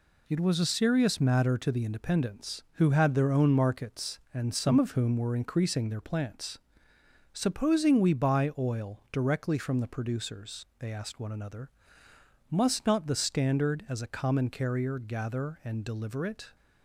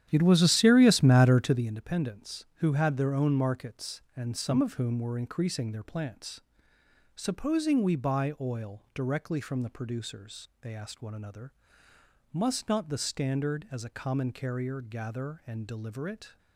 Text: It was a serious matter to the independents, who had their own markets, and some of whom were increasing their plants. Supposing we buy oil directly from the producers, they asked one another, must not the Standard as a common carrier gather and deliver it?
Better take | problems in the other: first | starts louder than the rest; strong; until 1.7 s; 10.5 dB

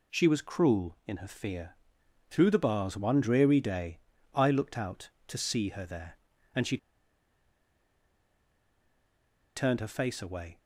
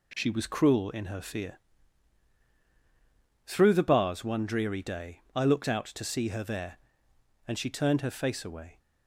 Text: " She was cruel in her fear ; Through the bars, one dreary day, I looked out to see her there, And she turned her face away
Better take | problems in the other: second | pauses between "she" and "turned"; strong; at 6.7 s; 2.7 s long

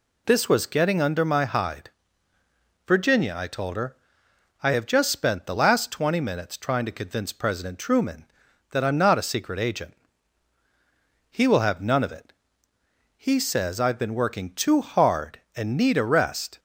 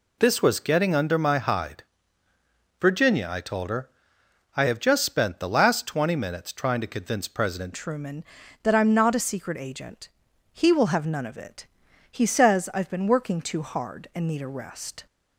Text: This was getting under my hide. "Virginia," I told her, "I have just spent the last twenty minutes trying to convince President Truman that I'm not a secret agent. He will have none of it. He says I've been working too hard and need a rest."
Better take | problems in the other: first | changes voice at "Truman"; from 7.7 s on; 7.3 s long

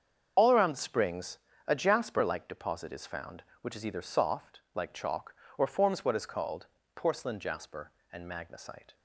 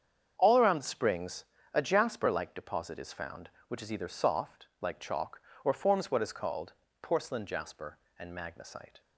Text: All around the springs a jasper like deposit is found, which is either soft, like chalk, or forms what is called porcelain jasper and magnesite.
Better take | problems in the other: second | loses the start of "All"; at 0.3 s; 55 ms // starts louder than the rest; until 1.6 s; 7 dB; strong in the second // pauses between "springs" and "a"; slight; at 1.3 s; 0.28 s long; slight in the second // pauses between "called" and "porcelain"; slight; at 6.6 s; 0.30 s long; slight in the second

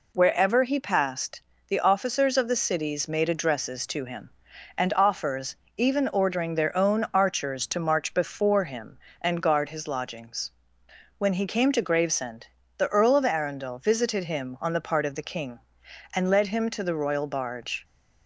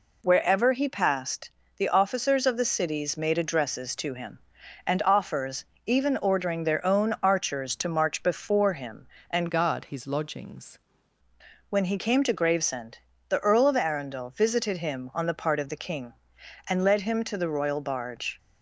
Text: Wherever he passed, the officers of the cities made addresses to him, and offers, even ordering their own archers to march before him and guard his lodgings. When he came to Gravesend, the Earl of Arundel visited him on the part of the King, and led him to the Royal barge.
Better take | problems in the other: first | changes voice from "guard" to "lodgings"; from 9.4 to 10.7 s; 1.3 s long

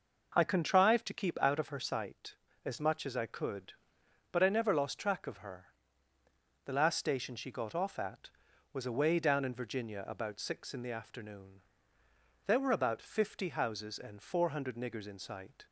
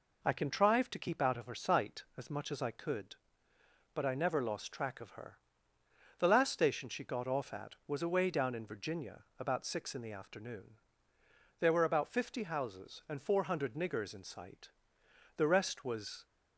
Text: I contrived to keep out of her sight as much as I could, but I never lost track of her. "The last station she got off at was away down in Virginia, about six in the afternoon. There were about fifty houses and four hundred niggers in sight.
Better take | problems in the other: first | goes on to say "The rest was"; noticeable; from 15.3 s on; 0.88 s long

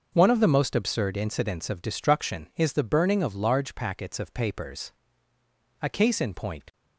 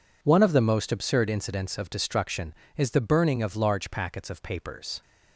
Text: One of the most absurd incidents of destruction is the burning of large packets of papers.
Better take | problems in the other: second | starts louder than the rest; until 1.1 s; 6 dB // goes on to say "A case in point"; noticeable; from 5.8 s on; 0.92 s long

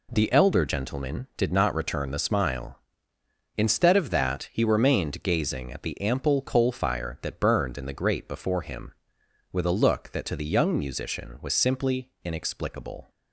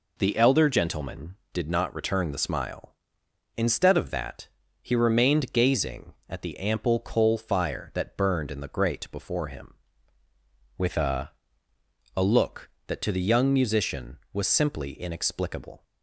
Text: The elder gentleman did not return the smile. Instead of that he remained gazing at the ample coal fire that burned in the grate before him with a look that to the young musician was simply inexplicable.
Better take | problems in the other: first | pauses between "that" and "he"; slight; at 4.4 s; 0.32 s long // says "a" twice; at 12.1 s

